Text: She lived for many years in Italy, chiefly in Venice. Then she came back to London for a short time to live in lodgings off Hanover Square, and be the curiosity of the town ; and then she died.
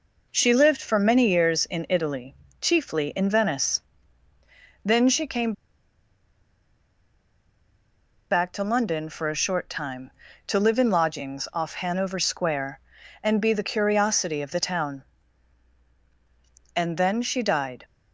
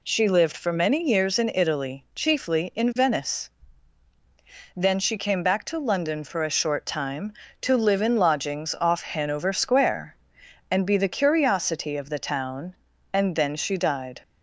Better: second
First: pauses between "came" and "back"; strong; at 5.5 s; 2.7 s long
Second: none

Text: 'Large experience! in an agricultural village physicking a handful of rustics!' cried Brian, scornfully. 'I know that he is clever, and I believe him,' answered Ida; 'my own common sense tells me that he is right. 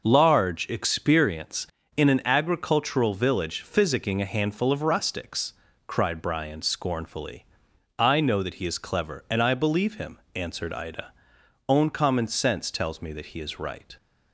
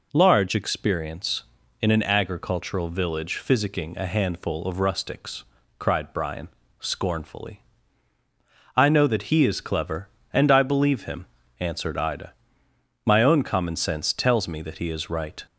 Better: second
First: skips "my"; at 11.4 s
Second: none

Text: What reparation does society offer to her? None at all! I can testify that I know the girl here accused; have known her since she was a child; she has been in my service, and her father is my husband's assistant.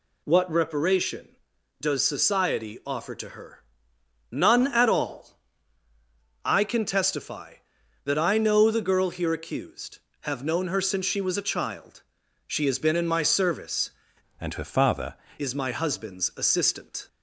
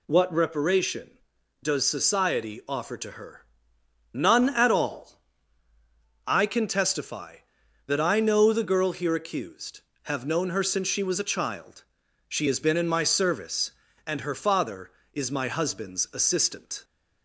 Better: second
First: changes voice from "and" to "father"; from 14.4 to 15.1 s; 0.7 s long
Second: none

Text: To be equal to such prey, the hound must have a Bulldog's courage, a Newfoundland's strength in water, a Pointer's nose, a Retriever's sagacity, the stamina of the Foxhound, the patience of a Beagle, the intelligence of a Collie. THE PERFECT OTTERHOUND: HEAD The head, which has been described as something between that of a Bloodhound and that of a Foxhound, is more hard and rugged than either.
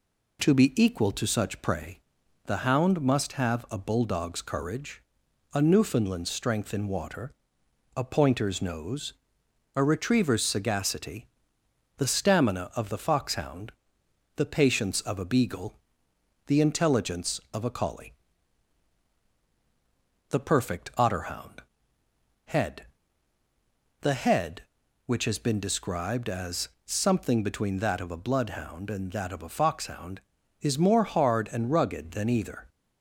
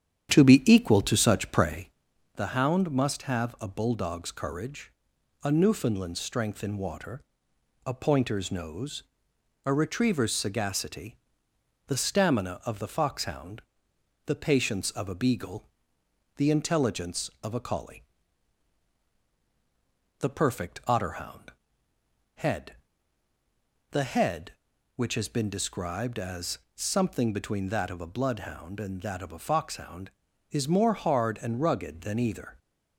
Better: first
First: pauses between "HEAD" and "The"; at 22.8 s; 1.1 s long // pauses between "as" and "something"; slight; at 26.6 s; 0.18 s long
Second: starts louder than the rest; strong; until 2.1 s; 9 dB // pauses between "HEAD" and "The"; at 22.7 s; 1.1 s long // pauses between "as" and "something"; slight; at 26.5 s; 0.18 s long

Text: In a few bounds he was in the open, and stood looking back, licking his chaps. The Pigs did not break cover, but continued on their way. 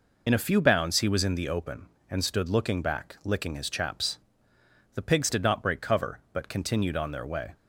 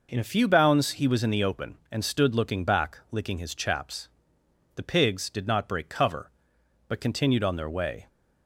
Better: second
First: loses the start of "In"; at 0.2 s; 65 ms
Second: none

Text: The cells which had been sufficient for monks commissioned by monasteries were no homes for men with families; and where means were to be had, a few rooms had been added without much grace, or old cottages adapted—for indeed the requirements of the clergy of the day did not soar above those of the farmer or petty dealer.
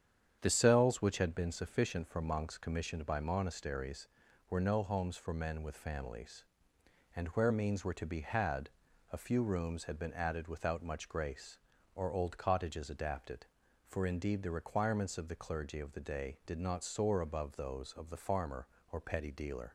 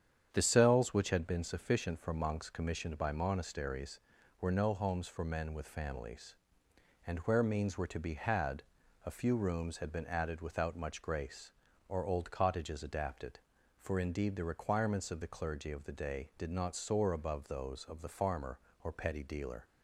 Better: neither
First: starts louder than the rest; strong; until 1.4 s; 8.5 dB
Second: starts louder than the rest; strong; until 1.3 s; 8.5 dB

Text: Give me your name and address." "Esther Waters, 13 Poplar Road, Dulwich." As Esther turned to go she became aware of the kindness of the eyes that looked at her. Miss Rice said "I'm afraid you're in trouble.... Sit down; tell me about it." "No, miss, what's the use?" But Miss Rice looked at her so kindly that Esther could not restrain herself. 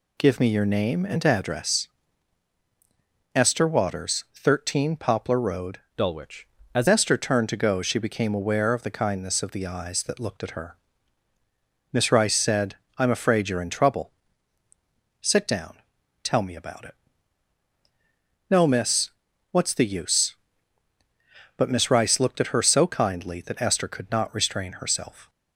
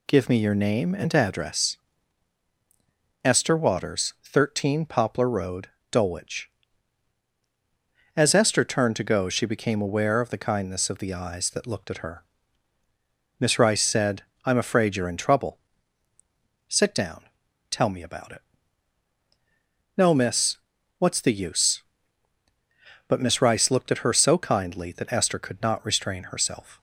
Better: second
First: changes voice from "Dulwich" to "As"; from 5.9 to 6.8 s; 0.9 s long // pauses between "said" and "I'm"; slight; at 12.7 s; 0.20 s long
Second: pauses between "said" and "I'm"; slight; at 14.2 s; 0.20 s long

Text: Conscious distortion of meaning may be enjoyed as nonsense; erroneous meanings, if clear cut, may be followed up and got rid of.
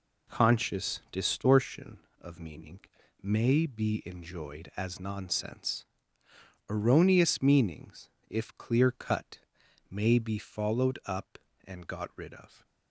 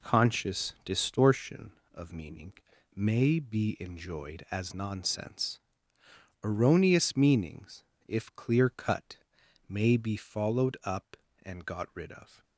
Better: neither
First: pauses between "meaning" and "may"; at 2.8 s; 0.42 s long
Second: pauses between "meaning" and "may"; at 2.5 s; 0.42 s long

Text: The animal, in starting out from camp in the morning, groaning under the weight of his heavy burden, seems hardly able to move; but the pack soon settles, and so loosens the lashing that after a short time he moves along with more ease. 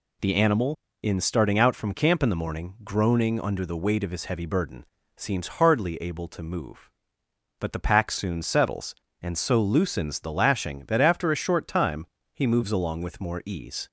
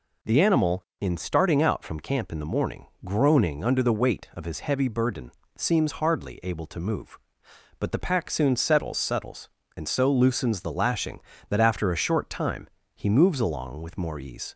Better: first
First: pauses between "time" and "he"; slight; at 12.0 s; 0.28 s long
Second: says "settles" twice; at 8.9 s // pauses between "time" and "he"; slight; at 12.6 s; 0.24 s long

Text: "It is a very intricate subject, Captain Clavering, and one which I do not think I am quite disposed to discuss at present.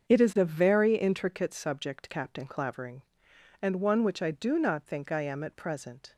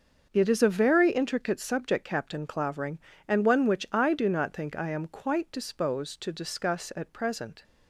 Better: second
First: starts louder than the rest; until 1.1 s; 7 dB // skips "quite disposed to discuss"; at 5.4 s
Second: starts louder than the rest; until 1.3 s; 6 dB

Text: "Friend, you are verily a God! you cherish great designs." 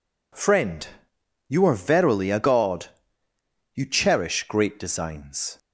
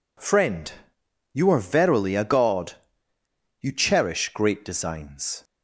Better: neither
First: none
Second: none

